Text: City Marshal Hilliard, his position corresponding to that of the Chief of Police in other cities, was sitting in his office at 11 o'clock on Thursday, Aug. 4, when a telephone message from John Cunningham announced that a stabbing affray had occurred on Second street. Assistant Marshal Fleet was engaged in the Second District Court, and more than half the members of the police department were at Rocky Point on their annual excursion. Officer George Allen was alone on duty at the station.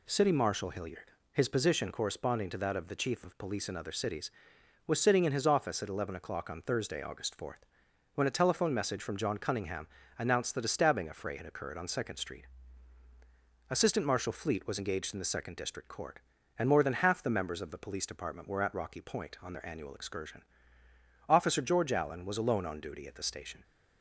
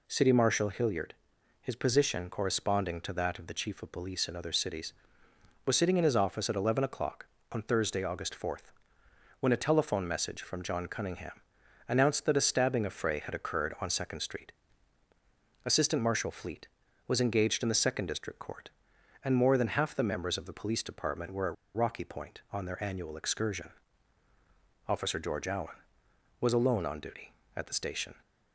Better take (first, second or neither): first